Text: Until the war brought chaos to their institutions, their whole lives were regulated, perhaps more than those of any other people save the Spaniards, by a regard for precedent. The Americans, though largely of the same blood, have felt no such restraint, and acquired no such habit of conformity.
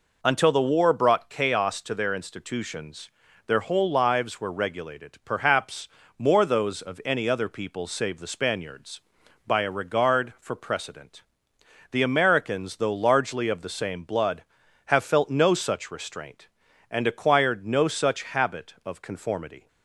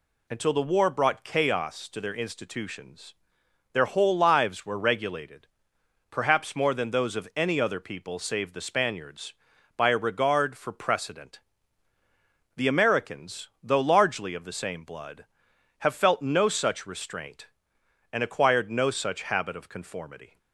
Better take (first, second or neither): second